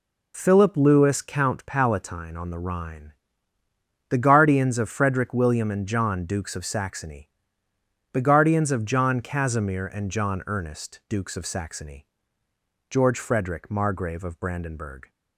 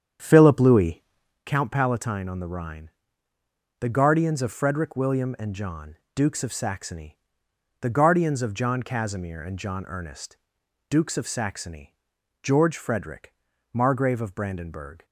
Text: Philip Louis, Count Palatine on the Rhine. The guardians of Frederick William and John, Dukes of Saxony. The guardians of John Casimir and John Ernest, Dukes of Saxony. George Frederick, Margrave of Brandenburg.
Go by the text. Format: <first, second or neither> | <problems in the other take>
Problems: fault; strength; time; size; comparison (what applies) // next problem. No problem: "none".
first | starts louder than the rest; strong; until 1.4 s; 8.5 dB